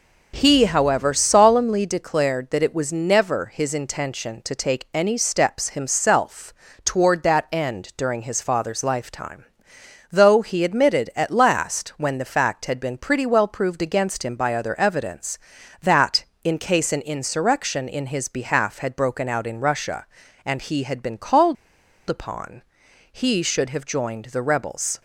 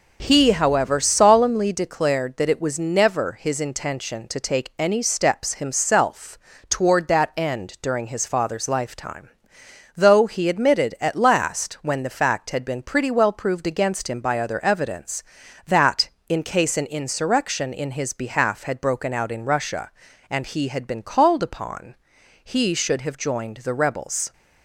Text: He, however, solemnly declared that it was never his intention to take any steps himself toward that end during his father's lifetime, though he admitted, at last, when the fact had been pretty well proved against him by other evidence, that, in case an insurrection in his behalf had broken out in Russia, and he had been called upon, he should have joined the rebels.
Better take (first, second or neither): second